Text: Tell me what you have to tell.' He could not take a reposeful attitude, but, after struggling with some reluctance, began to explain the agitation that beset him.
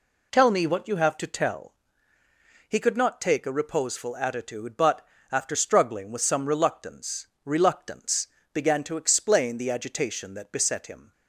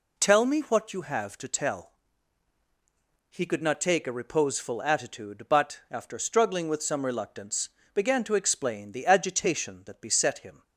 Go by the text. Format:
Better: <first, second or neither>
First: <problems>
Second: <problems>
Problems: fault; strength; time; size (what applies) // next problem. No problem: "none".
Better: second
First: says "reluctance" twice; at 7.4 s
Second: none